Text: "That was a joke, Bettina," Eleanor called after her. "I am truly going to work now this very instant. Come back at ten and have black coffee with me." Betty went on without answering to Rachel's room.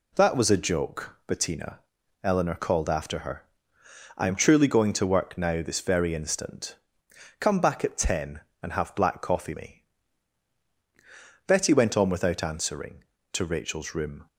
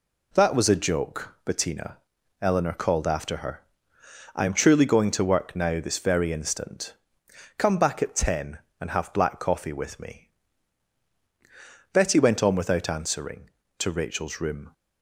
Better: second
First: skips "with"; at 9.5 s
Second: none

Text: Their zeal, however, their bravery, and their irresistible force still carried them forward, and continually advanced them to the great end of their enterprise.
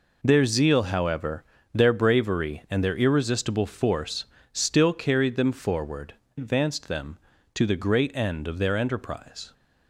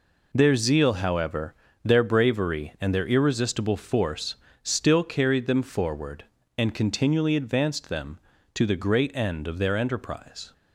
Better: second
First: pauses between "force" and "still"; slight; at 4.2 s; 0.28 s long // skips "and continually"; at 6.2 s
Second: pauses between "force" and "still"; slight; at 4.3 s; 0.28 s long

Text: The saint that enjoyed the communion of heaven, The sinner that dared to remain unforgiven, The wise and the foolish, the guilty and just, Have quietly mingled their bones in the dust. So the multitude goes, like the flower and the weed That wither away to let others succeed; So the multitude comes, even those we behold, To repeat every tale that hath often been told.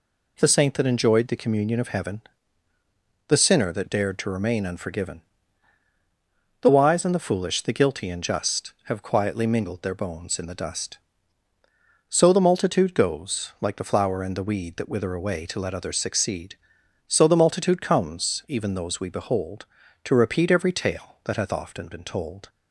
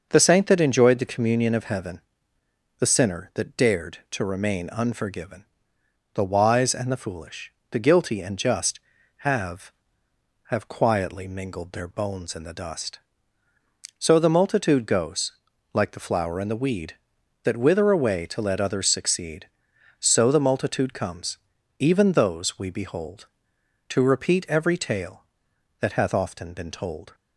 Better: first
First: none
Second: says "Have" twice; at 10.4 s

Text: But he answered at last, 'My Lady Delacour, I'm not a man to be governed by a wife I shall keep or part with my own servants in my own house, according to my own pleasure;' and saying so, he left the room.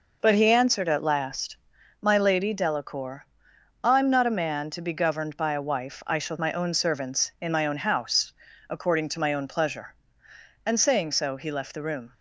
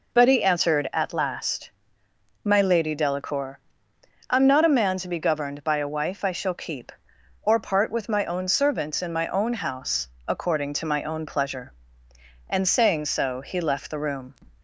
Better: second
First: skips "keep or part with"; at 6.3 s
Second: none

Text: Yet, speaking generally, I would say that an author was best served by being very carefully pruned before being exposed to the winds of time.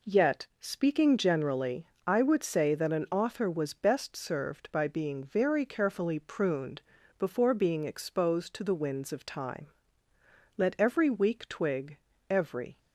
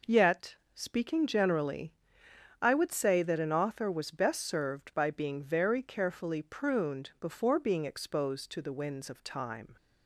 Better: second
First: pauses between "pruned" and "before"; at 6.8 s; 0.38 s long // goes on to say "Let every weak twig every"; strong; from 10.5 s on; 2.2 s long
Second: none

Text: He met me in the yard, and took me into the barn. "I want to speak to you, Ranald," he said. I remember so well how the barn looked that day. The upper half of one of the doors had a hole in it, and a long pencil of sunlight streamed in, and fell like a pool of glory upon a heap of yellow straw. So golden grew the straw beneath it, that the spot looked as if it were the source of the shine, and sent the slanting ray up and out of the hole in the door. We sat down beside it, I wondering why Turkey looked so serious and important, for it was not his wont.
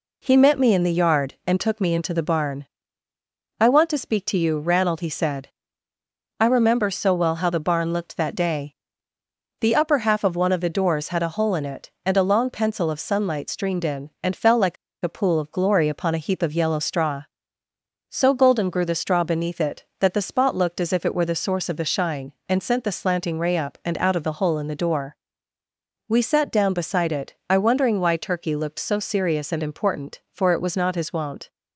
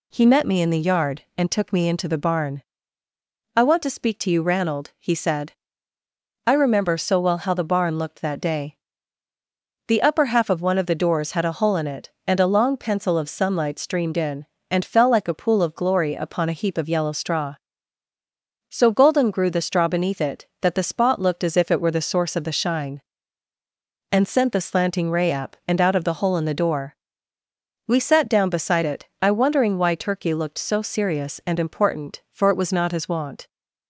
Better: second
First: pauses between "like" and "a"; slight; at 14.7 s; 0.27 s long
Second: none

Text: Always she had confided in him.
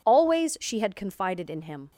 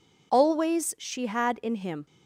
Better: first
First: none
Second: skips "confided"; at 1.6 s

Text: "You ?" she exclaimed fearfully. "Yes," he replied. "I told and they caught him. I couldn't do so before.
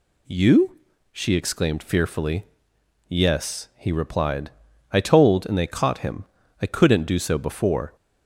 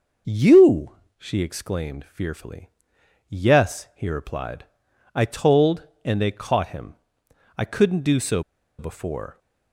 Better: first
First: none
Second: pauses between "so" and "before"; at 8.4 s; 0.37 s long

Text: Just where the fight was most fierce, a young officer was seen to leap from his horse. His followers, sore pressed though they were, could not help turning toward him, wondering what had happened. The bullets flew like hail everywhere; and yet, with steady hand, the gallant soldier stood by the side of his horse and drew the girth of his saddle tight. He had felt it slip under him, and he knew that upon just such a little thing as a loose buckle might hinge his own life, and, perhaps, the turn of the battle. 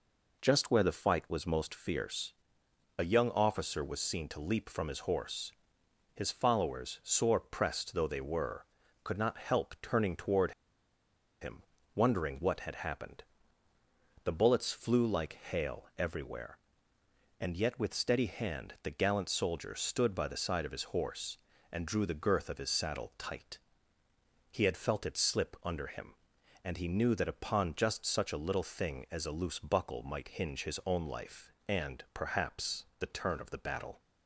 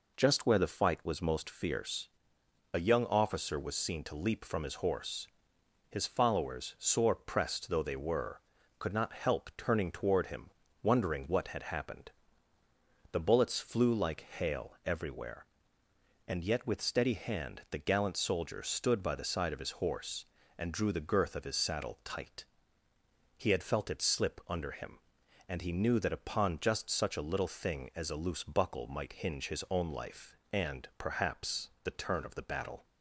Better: second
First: pauses between "toward" and "him"; noticeable; at 10.5 s; 0.89 s long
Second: none

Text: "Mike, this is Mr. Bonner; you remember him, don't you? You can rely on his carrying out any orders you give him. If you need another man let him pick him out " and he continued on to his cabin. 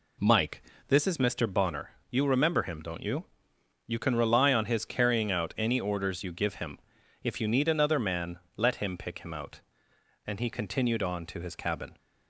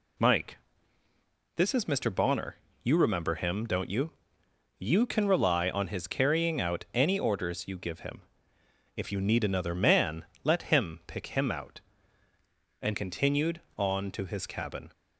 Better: first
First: pauses between "man" and "let"; slight; at 8.4 s; 0.16 s long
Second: pauses between "man" and "let"; slight; at 10.2 s; 0.18 s long // skips "he"; at 12.9 s

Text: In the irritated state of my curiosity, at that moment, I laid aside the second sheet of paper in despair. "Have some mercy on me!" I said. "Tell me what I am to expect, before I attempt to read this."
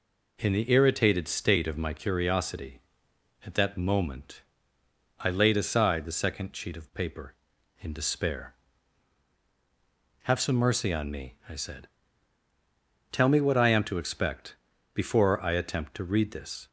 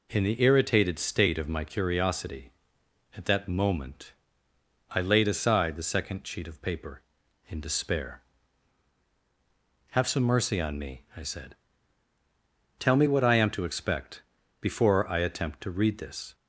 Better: neither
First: none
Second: none

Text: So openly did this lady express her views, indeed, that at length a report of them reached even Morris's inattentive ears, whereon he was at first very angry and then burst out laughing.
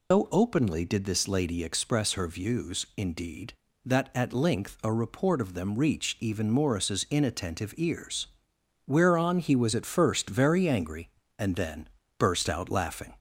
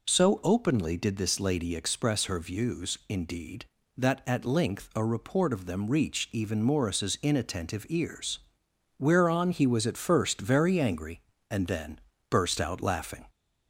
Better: second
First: loses the start of "So"; at 0.1 s; 160 ms // pauses between "then" and "burst"; slight; at 11.8 s; 0.30 s long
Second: pauses between "then" and "burst"; slight; at 11.9 s; 0.30 s long

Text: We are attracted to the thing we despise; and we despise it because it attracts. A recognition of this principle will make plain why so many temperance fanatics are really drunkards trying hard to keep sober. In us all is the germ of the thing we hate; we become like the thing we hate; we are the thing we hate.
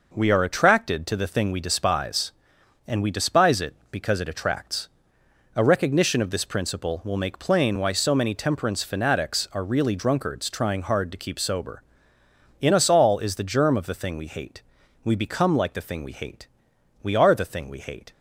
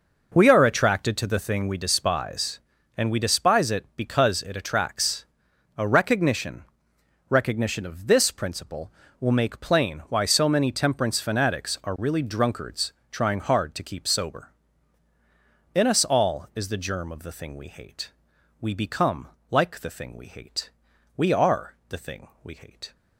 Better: first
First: none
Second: says "recognition" twice; at 7.2 s // pauses between "drunkards" and "trying"; slight; at 12.9 s; 0.22 s long // pauses between "become" and "like"; slight; at 19.2 s; 0.22 s long // pauses between "are" and "the"; slight; at 21.7 s; 0.16 s long // pauses between "thing" and "we"; slight; at 22.2 s; 0.16 s long

